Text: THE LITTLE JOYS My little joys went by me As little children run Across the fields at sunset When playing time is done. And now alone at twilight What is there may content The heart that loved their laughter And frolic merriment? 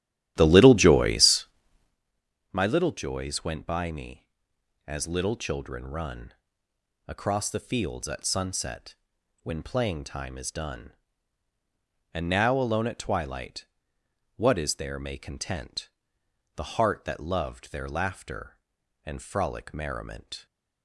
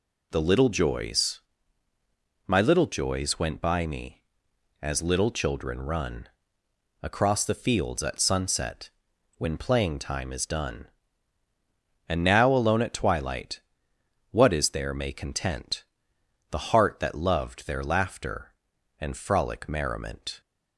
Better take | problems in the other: second | starts louder than the rest; strong; until 2.0 s; 12.5 dB // pauses between "JOYS" and "My"; at 1.4 s; 1.0 s long; also in the second // pauses between "run" and "Across"; noticeable; at 6.3 s; 0.74 s long; noticeable in the second // pauses between "sunset" and "When"; noticeable; at 8.9 s; 0.48 s long; noticeable in the second // pauses between "twilight" and "What"; noticeable; at 13.6 s; 0.72 s long; noticeable in the second // pauses between "content" and "The"; noticeable; at 15.8 s; 0.66 s long; noticeable in the second

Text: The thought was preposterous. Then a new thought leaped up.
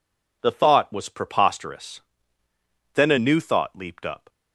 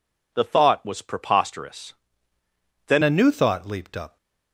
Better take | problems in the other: first | changes voice at "a"; from 3.0 s on; 1.1 s long

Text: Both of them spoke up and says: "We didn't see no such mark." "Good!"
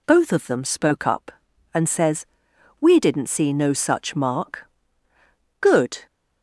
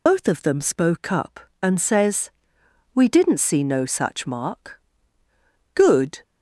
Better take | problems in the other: first | loses the start of "Both"; at 0.0 s; 70 ms

